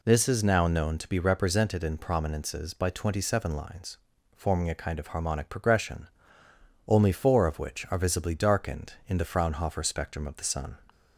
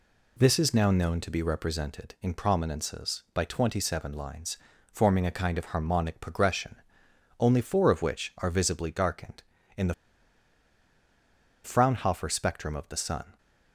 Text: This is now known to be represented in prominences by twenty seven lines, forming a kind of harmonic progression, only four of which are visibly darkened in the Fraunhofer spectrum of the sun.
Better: first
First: none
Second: pauses between "the" and "Fraunhofer"; strong; at 9.9 s; 1.7 s long

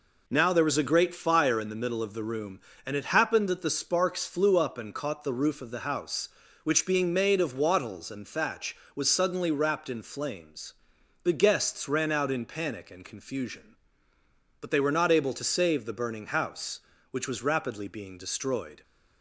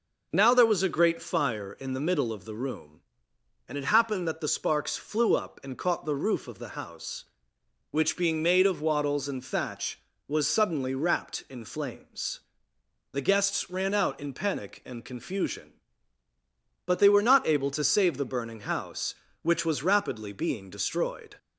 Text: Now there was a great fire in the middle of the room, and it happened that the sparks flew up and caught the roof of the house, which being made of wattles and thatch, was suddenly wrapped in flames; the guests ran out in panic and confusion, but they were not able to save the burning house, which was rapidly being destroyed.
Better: neither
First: none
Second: none

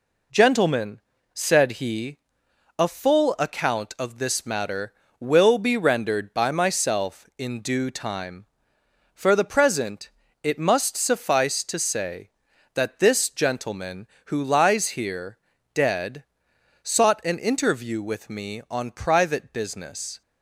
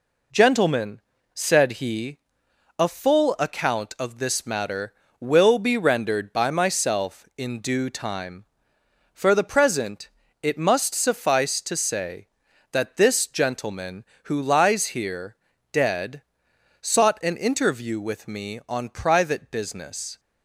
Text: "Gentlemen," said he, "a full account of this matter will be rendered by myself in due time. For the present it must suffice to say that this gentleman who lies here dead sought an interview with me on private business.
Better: neither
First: pauses between "present" and "it"; slight; at 10.0 s; 0.32 s long // pauses between "here" and "dead"; at 15.3 s; 0.38 s long // pauses between "dead" and "sought"; noticeable; at 16.2 s; 0.58 s long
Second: pauses between "present" and "it"; slight; at 10.0 s; 0.32 s long // pauses between "here" and "dead"; at 15.3 s; 0.38 s long // pauses between "dead" and "sought"; noticeable; at 16.2 s; 0.58 s long

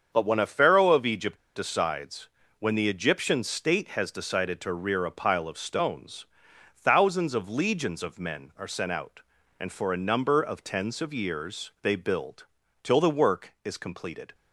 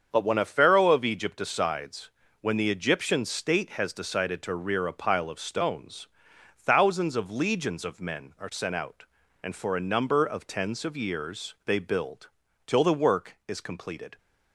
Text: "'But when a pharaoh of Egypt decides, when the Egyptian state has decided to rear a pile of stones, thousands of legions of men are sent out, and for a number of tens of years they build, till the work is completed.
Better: second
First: starts louder than the rest; strong; until 1.1 s; 7 dB // pauses between "Egypt" and "decides"; slight; at 1.3 s; 0.18 s long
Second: starts louder than the rest; strong; until 1.1 s; 7 dB

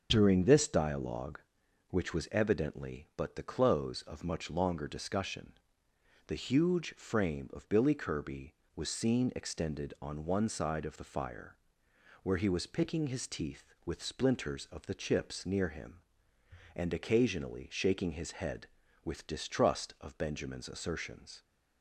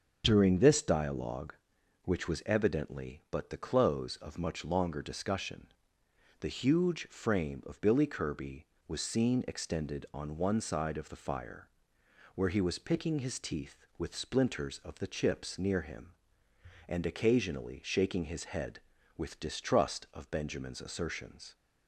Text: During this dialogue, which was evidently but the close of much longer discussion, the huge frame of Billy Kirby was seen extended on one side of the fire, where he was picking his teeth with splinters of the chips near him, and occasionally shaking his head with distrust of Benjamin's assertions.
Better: neither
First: starts louder than the rest; until 1.1 s; 7 dB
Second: starts louder than the rest; until 1.2 s; 7 dB

